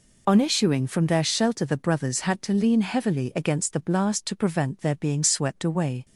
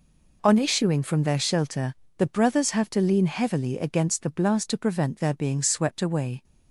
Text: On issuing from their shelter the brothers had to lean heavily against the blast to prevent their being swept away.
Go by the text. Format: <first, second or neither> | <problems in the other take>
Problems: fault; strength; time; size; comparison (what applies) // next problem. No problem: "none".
first | pauses between "shelter" and "the"; slight; at 1.9 s; 0.22 s long // says "have" for "had"; at 2.7 s